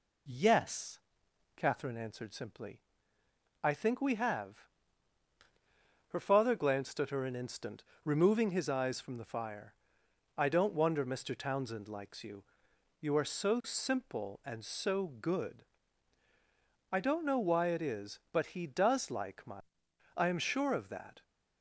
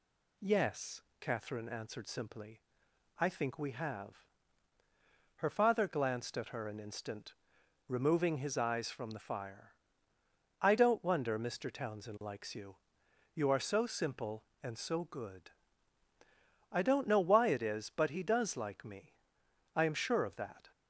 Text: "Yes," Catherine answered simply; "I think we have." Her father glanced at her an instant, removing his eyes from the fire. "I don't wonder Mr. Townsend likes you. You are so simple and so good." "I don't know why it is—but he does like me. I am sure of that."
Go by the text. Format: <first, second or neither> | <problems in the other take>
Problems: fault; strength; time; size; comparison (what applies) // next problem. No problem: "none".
second | says "my" for "me"; at 19.4 s